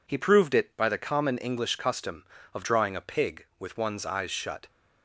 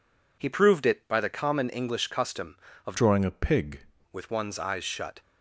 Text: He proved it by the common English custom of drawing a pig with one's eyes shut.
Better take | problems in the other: first | changes voice from "drawing" to "pig"; from 2.9 to 3.8 s; 0.9 s long

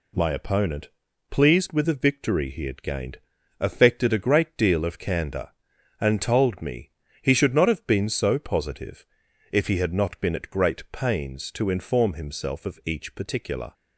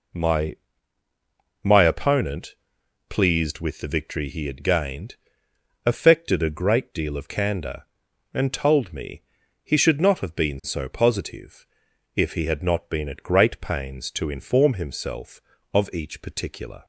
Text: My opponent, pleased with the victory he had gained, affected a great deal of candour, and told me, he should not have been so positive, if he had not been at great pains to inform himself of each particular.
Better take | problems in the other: first | says "My" twice; at 1.6 s

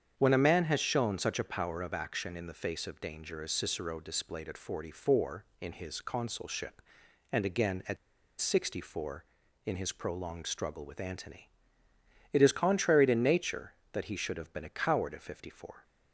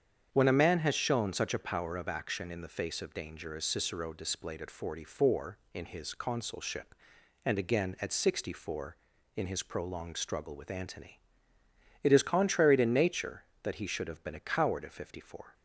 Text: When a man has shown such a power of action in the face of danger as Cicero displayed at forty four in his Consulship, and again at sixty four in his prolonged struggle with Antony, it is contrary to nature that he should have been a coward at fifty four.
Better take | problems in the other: second | starts louder than the rest; strong; until 1.1 s; 8 dB; strong in the second // pauses between "at" and "sixty"; at 7.9 s; 0.44 s long

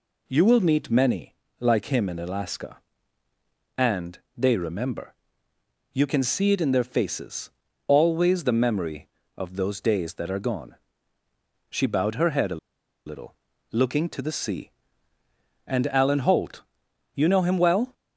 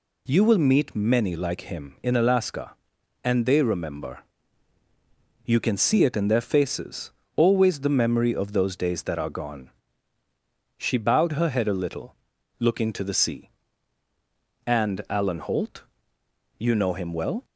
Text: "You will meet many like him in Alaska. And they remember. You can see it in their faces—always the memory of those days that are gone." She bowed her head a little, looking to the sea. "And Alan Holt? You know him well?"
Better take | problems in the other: second | pauses between "many" and "like"; slight; at 1.3 s; 0.24 s long // pauses between "And" and "they"; slight; at 4.1 s; 0.18 s long // pauses between "a" and "little"; noticeable; at 12.5 s; 0.47 s long

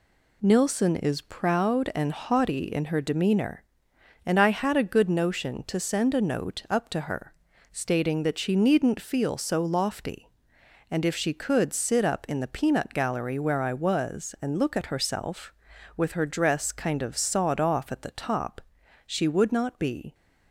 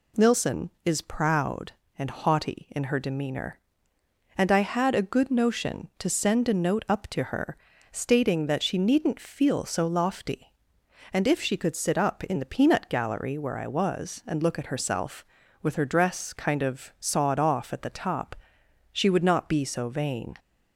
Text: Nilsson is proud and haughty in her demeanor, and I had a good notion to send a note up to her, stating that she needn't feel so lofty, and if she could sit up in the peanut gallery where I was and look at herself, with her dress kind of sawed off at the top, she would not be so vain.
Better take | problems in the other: second | stops before "so vain"; at 20.1 s

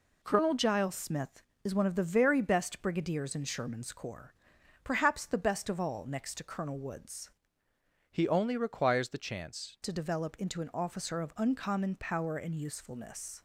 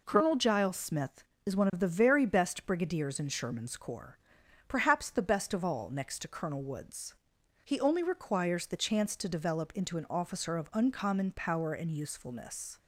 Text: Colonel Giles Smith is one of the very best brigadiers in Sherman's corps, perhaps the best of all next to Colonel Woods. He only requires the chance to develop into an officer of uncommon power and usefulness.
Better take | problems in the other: second | changes voice from "He" to "chance"; from 8.1 to 9.7 s; 1.6 s long

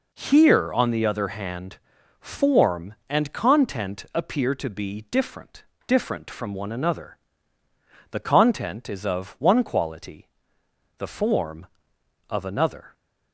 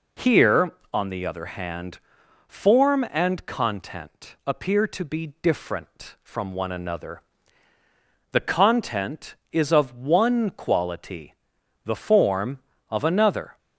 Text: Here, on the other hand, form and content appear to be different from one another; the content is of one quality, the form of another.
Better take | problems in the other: second | says "different" twice; at 5.8 s

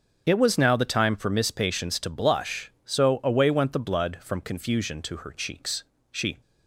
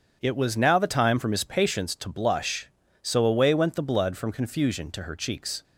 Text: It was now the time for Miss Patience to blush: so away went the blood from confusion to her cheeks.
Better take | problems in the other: second | starts louder than the rest; strong; until 1.2 s; 7 dB; strong in the second // goes on to say "She"; slight; from 6.1 s on; 0.30 s long

